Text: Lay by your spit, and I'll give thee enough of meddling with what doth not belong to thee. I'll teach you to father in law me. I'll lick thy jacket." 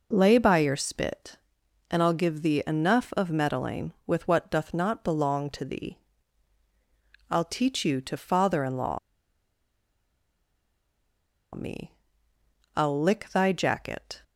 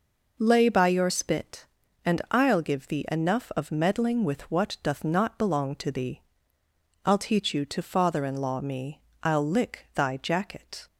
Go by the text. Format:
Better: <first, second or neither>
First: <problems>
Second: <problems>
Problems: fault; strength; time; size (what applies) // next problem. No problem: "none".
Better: second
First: pauses between "law" and "me"; strong; at 8.9 s; 2.5 s long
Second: none